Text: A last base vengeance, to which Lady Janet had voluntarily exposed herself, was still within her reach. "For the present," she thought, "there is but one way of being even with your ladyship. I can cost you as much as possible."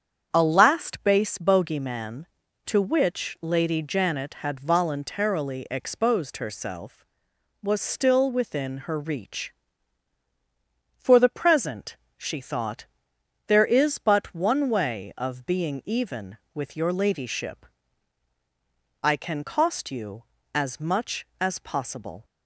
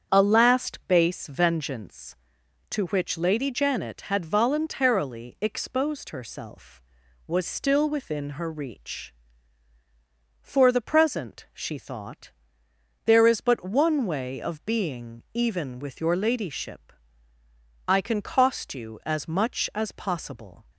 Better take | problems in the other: second | starts louder than the rest; strong; until 1.3 s; 8 dB; strong in the second // says "bogeyman" for "vengeance"; at 1.3 s

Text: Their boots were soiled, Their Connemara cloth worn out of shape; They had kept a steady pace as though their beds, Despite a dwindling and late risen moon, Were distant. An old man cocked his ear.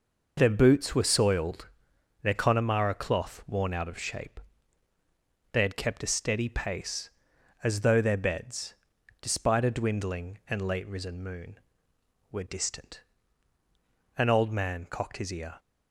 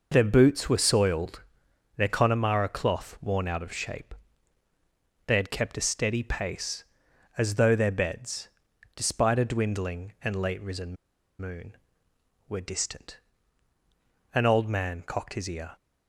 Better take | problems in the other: first | pauses between "risen" and "moon"; at 10.9 s; 0.45 s long

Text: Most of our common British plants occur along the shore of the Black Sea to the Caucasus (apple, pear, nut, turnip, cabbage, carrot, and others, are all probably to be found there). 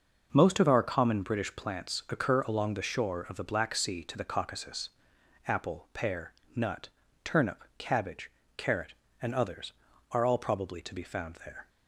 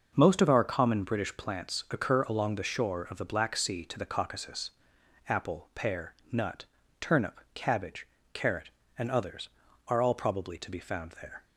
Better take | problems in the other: neither | none

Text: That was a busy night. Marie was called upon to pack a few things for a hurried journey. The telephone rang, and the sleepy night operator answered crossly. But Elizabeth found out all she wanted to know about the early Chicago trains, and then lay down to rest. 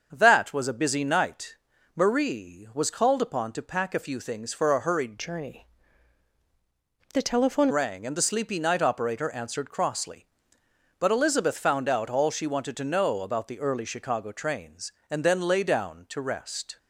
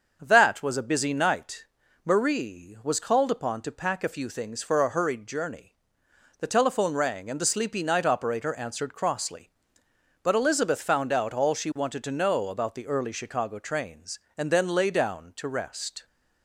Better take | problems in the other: second | starts louder than the rest; until 1.1 s; 6.5 dB; also in the second // changes voice from "journey" to "telephone"; from 5.1 to 7.6 s; 2.5 s long

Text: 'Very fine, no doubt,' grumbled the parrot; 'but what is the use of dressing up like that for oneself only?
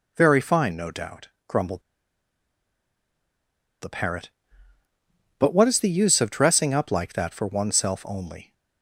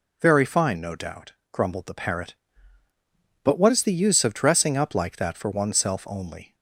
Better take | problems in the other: second | pauses between "grumbled" and "the"; strong; at 1.8 s; 2.0 s long

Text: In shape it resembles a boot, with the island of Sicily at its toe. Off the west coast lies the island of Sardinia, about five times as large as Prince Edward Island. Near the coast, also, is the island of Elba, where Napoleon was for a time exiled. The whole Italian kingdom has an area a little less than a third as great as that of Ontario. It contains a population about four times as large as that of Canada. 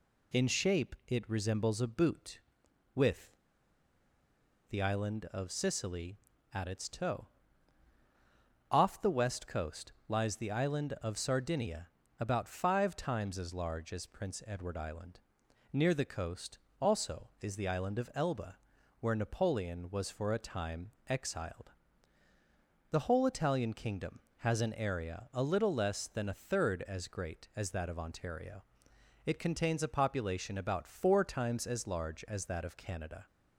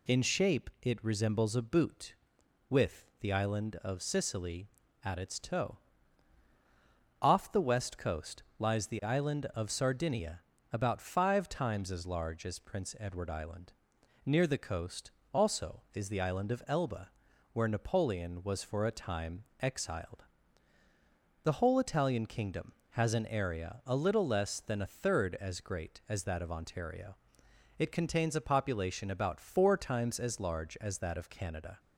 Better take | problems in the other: second | pauses between "with" and "the"; strong; at 3.3 s; 1.3 s long // pauses between "time" and "exiled"; slight; at 20.9 s; 0.18 s long; slight in the second

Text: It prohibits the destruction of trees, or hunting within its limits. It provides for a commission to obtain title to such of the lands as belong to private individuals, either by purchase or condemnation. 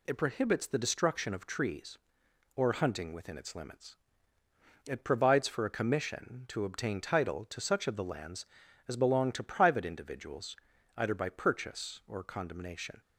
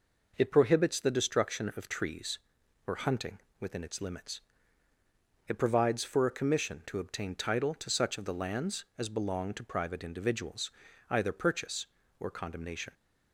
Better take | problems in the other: first | pauses between "hunting" and "within"; slight; at 3.3 s; 0.22 s long // skips "by"; at 11.3 s

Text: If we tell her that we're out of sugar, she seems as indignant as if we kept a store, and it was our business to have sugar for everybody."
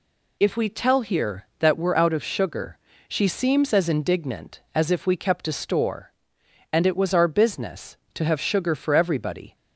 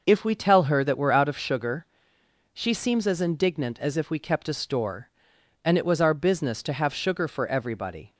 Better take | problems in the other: second | says "here" for "her"; at 1.0 s

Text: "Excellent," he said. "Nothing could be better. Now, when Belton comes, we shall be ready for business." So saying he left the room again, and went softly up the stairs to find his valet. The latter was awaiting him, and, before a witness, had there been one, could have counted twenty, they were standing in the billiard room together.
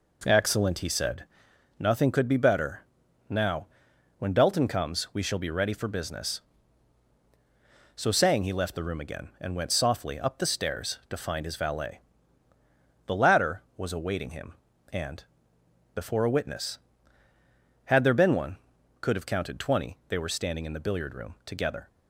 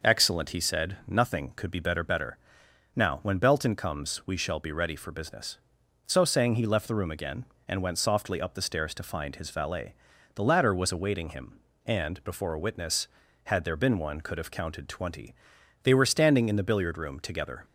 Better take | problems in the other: first | says "better" twice; at 2.0 s

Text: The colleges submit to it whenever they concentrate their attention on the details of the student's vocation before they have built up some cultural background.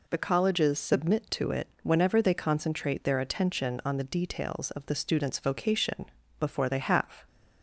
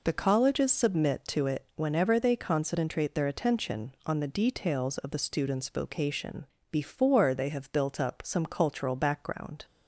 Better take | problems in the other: second | pauses between "it" and "whenever"; slight; at 1.6 s; 0.16 s long // pauses between "vocation" and "before"; slight; at 6.0 s; 0.34 s long; slight in the second // stops before "built up some cultural background"; at 7.2 s

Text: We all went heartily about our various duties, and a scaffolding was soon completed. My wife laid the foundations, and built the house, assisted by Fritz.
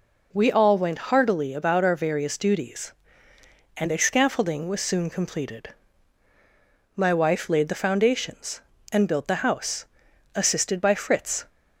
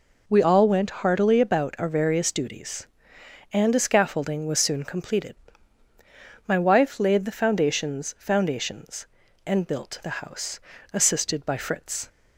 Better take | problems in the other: first | says "foundations" twice; at 8.1 s

